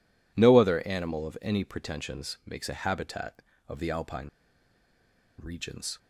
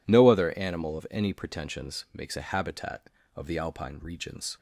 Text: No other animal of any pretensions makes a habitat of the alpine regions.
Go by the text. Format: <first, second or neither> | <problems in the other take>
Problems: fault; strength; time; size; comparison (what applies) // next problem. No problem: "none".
second | pauses between "alpine" and "regions"; at 4.2 s; 1.1 s long